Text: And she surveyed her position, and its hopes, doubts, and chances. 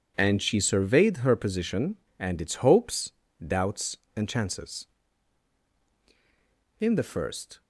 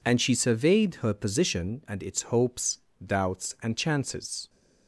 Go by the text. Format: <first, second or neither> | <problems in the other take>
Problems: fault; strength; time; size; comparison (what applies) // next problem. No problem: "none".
second | goes on to say "In the first"; noticeable; from 6.7 s on; 0.82 s long